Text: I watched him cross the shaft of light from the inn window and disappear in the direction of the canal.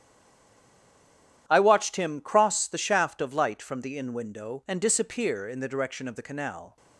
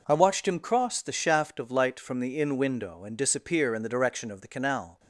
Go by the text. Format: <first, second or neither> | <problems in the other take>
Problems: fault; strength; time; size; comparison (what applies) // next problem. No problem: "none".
second | stays silent before the first word; noticeable; until 1.4 s; 1.4 s long // starts louder than the rest; strong; until 2.4 s; 11 dB